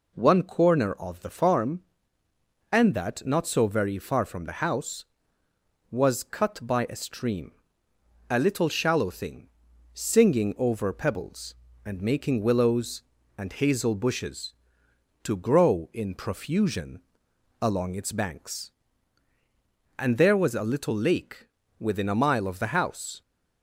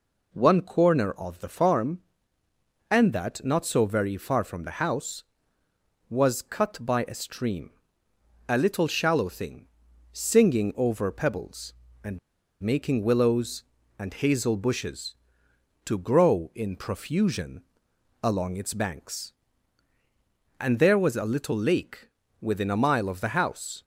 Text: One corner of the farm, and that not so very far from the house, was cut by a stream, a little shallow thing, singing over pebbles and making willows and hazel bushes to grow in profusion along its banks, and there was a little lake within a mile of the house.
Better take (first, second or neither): first